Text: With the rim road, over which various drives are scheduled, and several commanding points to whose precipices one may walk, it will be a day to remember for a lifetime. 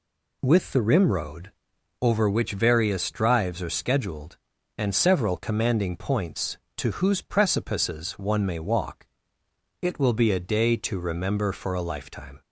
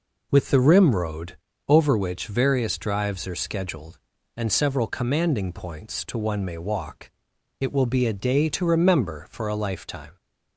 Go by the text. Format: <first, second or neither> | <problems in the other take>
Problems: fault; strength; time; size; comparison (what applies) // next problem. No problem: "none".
first | skips "whose precipices"; at 6.1 s